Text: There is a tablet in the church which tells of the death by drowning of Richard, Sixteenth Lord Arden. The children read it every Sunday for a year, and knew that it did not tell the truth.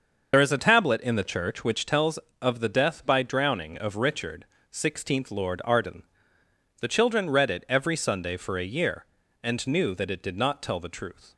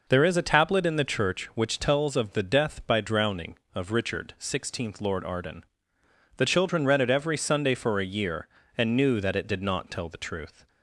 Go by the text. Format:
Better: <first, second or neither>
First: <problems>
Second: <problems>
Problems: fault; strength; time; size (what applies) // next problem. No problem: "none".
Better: second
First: loses the start of "There"; at 0.3 s; 55 ms // starts louder than the rest; noticeable; until 1.3 s; 6 dB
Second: none